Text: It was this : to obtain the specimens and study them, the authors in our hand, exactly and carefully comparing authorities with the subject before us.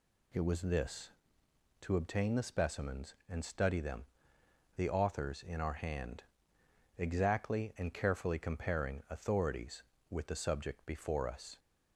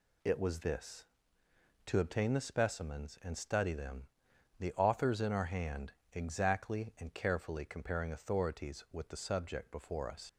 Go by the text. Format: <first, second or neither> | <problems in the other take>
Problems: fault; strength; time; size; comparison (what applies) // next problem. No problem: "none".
first | leaves "us" unfinished; at 10.2 s; 50 ms